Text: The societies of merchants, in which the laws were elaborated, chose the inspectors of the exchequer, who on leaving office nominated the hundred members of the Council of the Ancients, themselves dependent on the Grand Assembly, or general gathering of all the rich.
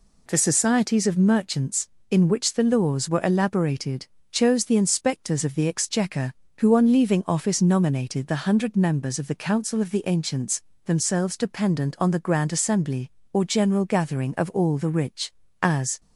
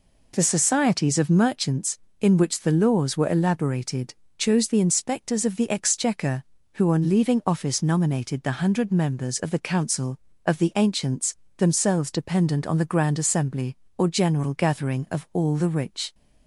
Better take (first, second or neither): second